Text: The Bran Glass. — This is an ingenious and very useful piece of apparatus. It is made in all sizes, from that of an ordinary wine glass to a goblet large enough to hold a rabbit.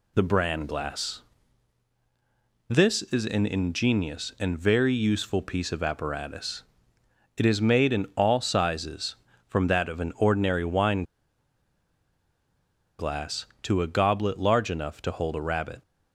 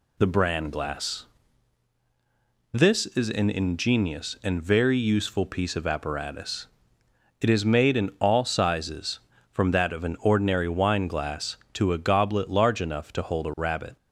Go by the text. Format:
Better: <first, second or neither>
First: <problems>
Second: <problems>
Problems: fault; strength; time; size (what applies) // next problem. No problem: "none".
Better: second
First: pauses between "wine" and "glass"; strong; at 11.0 s; 1.9 s long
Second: none